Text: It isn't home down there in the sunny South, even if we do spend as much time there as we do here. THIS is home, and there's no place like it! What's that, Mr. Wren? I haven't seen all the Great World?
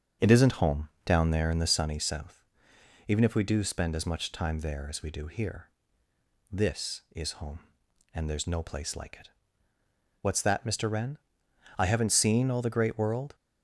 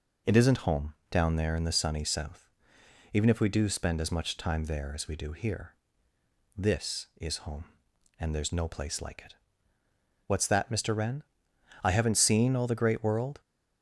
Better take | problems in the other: second | starts louder than the rest; until 1.9 s; 6.5 dB // pauses between "home" and "down"; slight; at 0.8 s; 0.16 s long; slight in the second

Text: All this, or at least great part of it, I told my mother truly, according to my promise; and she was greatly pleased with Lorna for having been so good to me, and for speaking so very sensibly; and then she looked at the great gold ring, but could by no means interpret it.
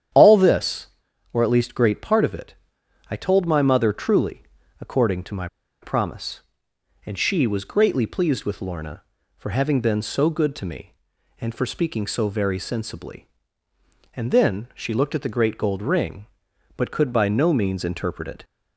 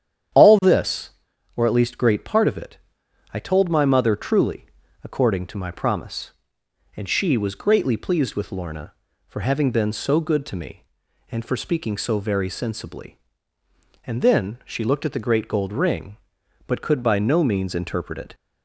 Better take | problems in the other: second | starts louder than the rest; strong; until 1.5 s; 9.5 dB; strong in the second // pauses between "my" and "promise"; slight; at 5.4 s; 0.35 s long

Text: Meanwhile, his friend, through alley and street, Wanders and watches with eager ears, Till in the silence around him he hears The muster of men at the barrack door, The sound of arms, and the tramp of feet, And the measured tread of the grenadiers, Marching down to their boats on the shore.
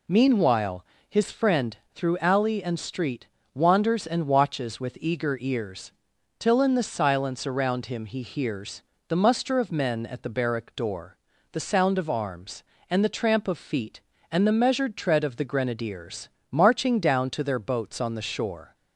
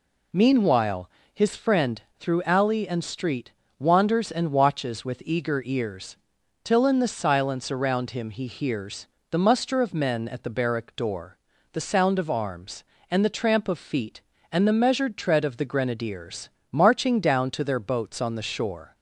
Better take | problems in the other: neither | pauses between "hears" and "The"; slight; the same in both

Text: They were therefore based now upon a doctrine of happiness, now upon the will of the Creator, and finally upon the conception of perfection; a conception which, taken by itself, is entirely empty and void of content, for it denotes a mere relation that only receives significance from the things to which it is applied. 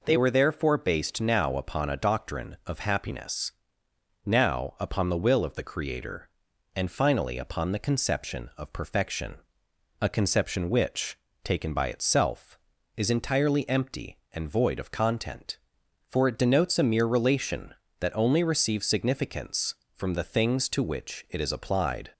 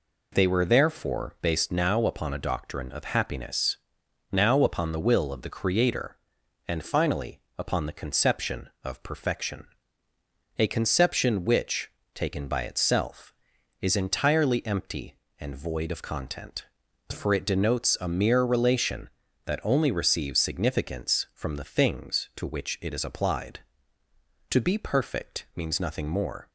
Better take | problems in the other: first | pauses between "finally" and "upon"; slight; at 7.4 s; 0.18 s long // goes on to say "To be perfect means nothing more"; strong; from 24.4 s on; 2.0 s long

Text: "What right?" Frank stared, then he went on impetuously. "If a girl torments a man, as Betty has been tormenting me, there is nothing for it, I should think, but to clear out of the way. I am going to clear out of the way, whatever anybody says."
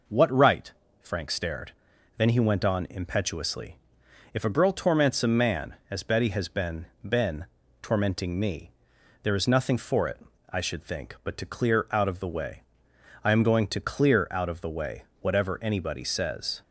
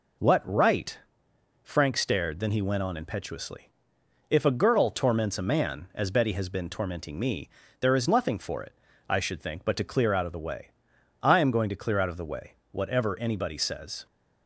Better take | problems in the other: second | says "been" twice; at 7.0 s

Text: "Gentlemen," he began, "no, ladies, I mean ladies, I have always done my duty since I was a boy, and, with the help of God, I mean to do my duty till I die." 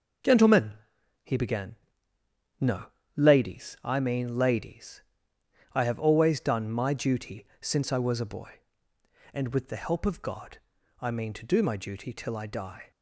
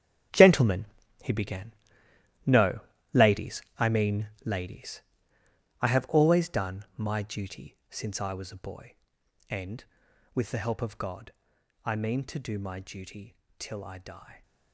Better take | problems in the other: first | gets quieter; strong; throughout; 12.5 dB // pauses between "mean" and "ladies"; slight; at 4.2 s; 0.16 s long // pauses between "duty" and "till"; slight; at 13.3 s; 0.22 s long

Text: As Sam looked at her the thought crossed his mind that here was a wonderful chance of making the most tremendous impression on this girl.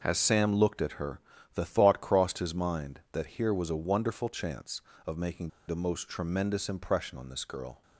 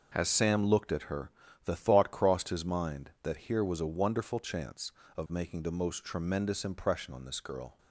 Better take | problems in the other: second | pauses between "her" and "the"; slight; at 1.2 s; 0.34 s long; slight in the second // pauses between "making" and "the"; slight; at 5.5 s; 0.17 s long

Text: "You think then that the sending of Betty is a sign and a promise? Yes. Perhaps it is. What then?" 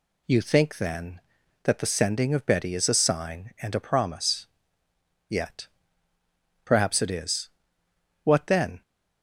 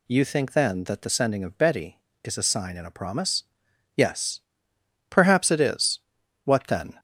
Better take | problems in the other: second | says "Yet" for "Yes"; at 5.2 s

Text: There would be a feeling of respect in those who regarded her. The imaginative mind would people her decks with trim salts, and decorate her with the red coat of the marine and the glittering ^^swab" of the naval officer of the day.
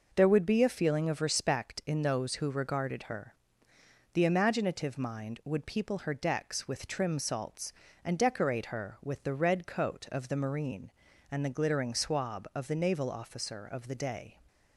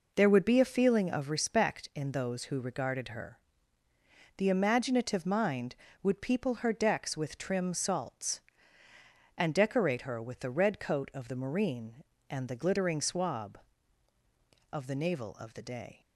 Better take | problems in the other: first | skips "officer"; at 15.3 s

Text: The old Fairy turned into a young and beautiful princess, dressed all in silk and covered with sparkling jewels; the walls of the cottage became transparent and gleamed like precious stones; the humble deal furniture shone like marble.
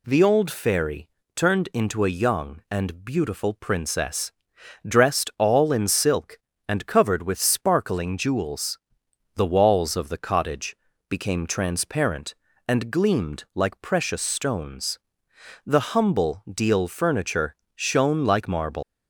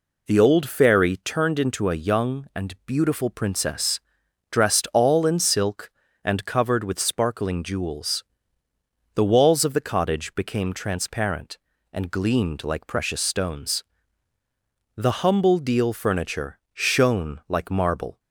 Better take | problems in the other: second | pauses between "Fairy" and "turned"; slight; at 1.0 s; 0.26 s long // pauses between "cottage" and "became"; slight; at 10.7 s; 0.32 s long // pauses between "furniture" and "shone"; slight; at 17.5 s; 0.20 s long // leaves "marble" unfinished; at 18.8 s; 115 ms

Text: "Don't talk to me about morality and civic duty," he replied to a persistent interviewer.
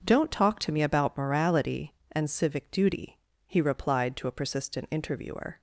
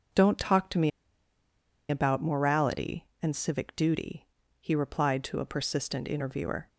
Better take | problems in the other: first | pauses between "me" and "about"; at 0.8 s; 0.99 s long

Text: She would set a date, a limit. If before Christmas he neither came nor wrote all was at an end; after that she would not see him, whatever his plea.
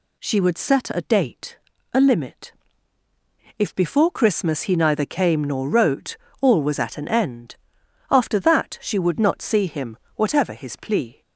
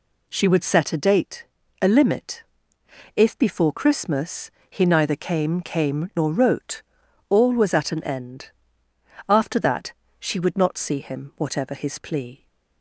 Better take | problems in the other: first | pauses between "Christmas" and "he"; slight; at 4.5 s; 0.18 s long // says "came" twice; at 5.6 s // pauses between "wrote" and "all"; noticeable; at 6.8 s; 0.46 s long; slight in the first // pauses between "that" and "she"; slight; at 9.9 s; 0.26 s long

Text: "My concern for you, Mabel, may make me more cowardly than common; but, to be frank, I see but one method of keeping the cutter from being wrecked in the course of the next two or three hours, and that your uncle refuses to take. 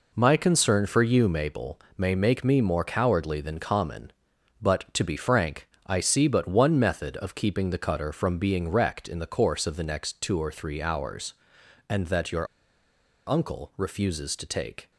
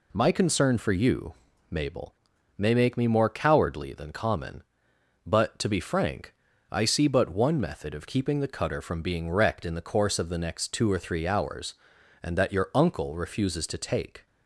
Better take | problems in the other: second | pauses between "your" and "uncle"; noticeable; at 12.4 s; 0.83 s long

